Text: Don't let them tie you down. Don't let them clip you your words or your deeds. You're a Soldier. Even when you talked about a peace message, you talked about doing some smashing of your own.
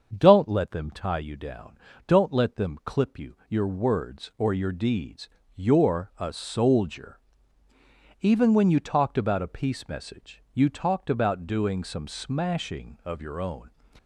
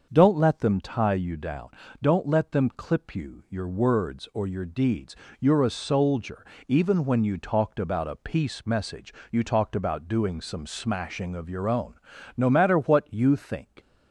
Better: first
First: starts louder than the rest; until 1.1 s; 7 dB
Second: starts louder than the rest; until 1.1 s; 6.5 dB // goes on to say "No matter what you think"; from 12.3 s on; 1.3 s long

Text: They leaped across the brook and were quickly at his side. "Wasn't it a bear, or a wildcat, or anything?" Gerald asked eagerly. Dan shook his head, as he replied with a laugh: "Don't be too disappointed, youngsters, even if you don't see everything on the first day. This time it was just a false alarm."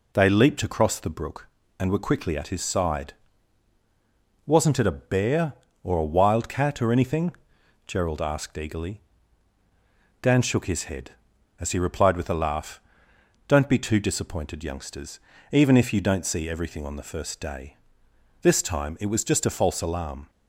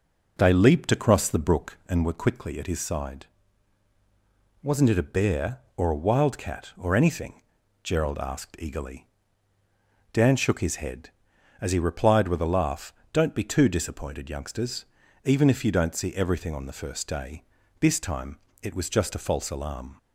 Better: first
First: none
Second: starts louder than the rest; noticeable; until 2.0 s; 5.5 dB // pauses between "time" and "it"; slight; at 18.3 s; 0.24 s long

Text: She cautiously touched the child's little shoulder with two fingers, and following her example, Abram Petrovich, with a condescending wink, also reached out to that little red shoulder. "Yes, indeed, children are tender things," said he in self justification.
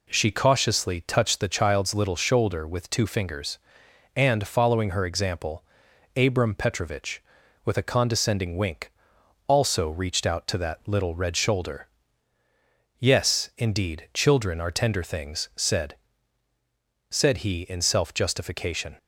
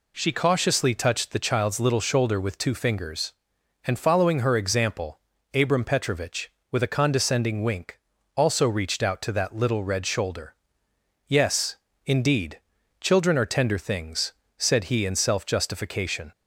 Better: second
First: says "said" twice; at 17.1 s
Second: none

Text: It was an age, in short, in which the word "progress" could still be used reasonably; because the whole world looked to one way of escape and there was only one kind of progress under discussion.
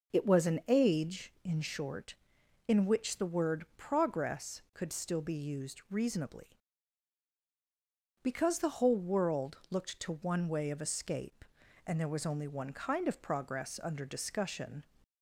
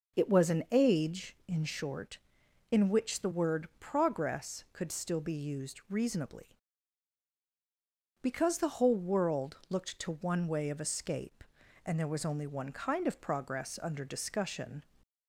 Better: neither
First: none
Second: none

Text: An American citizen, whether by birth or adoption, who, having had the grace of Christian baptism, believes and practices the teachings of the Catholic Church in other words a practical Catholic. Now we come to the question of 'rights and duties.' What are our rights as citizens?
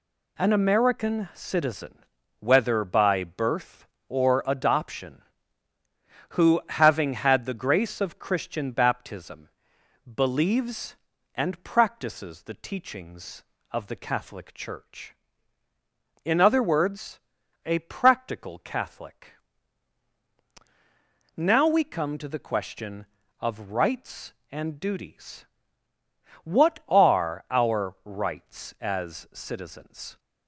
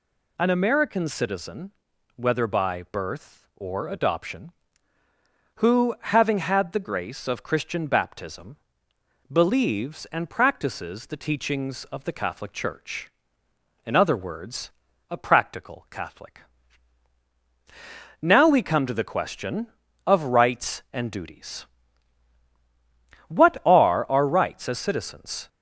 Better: neither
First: pauses between "words" and "a"; noticeable; at 17.1 s; 0.46 s long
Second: pauses between "words" and "a"; at 14.6 s; 0.40 s long

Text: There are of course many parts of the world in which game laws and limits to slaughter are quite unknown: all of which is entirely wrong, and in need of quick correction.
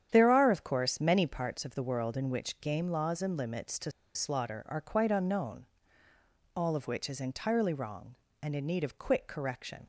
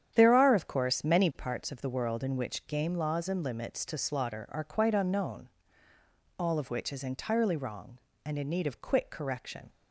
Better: second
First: starts louder than the rest; strong; until 1.1 s; 9 dB // pauses between "to" and "slaughter"; slight; at 3.9 s; 0.23 s long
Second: starts louder than the rest; strong; until 1.1 s; 9 dB

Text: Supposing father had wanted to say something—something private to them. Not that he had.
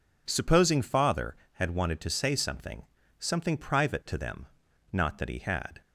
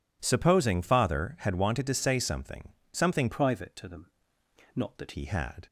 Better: first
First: none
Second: changes voice from "private" to "that"; from 3.3 to 5.1 s; 1.8 s long

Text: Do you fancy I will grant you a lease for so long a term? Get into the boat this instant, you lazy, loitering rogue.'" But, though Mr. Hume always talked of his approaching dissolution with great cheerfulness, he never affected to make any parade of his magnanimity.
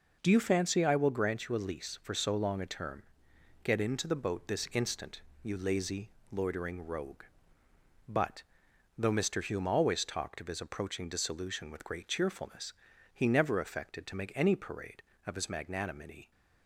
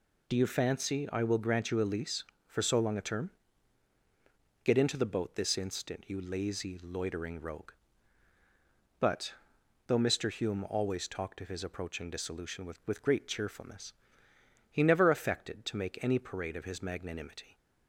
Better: first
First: none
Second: says "with" twice; at 12.8 s

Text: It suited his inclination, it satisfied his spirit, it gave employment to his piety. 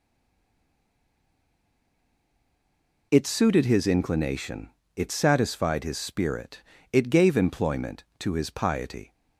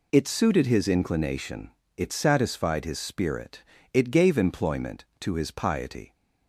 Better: second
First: stays silent before the first word; strong; until 3.1 s; 3.1 s long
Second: none

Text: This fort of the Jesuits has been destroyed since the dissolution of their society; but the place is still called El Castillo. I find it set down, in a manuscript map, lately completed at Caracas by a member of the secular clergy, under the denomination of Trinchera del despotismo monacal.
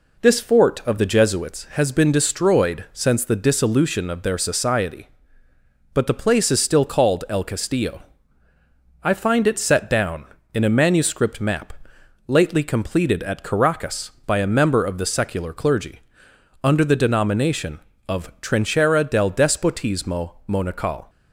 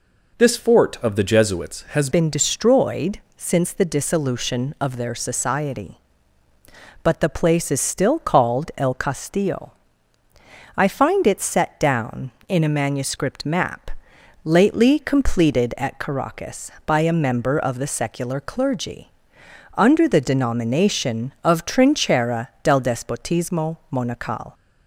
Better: first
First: pauses between "despotismo" and "monacal"; slight; at 20.3 s; 0.18 s long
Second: changes voice at "been"; from 2.1 s on; 22.4 s long // pauses between "destroyed" and "since"; slight; at 3.1 s; 0.16 s long // pauses between "Trinchera" and "del"; slight; at 22.4 s; 0.16 s long // pauses between "despotismo" and "monacal"; slight; at 23.7 s; 0.16 s long

